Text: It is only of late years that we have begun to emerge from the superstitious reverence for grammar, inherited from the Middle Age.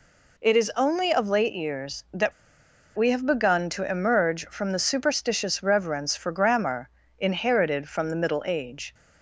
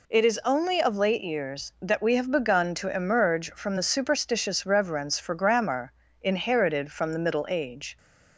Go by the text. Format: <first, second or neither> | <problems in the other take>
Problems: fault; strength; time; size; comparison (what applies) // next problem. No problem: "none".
second | pauses between "that" and "we"; noticeable; at 2.3 s; 0.66 s long